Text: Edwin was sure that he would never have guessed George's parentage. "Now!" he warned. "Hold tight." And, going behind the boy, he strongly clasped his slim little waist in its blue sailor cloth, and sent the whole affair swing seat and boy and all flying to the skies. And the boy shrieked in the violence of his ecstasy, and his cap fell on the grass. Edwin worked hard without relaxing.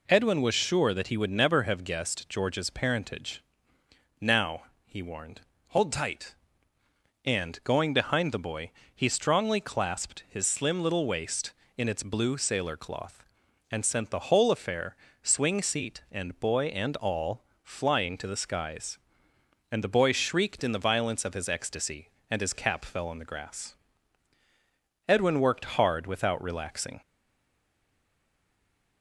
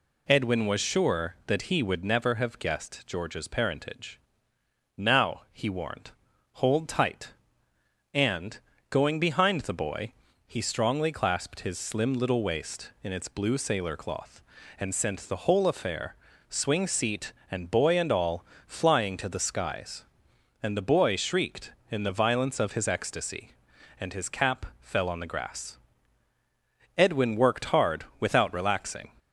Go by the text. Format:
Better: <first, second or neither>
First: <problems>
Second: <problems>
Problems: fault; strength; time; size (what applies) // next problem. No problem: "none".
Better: second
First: pauses between "affair" and "swing"; slight; at 14.9 s; 0.28 s long // pauses between "all" and "flying"; slight; at 17.4 s; 0.20 s long // stays silent after the last word; noticeable; from 27.0 s on; 2.0 s long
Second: pauses between "affair" and "swing"; slight; at 16.1 s; 0.32 s long // pauses between "all" and "flying"; slight; at 18.4 s; 0.22 s long